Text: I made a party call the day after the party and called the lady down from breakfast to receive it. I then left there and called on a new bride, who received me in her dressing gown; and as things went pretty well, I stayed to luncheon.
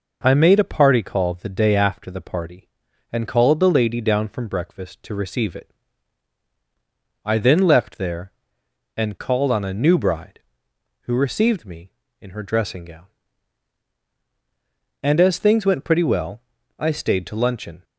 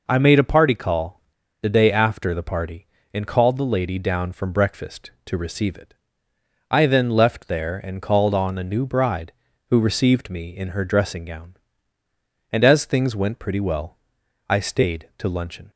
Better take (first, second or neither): first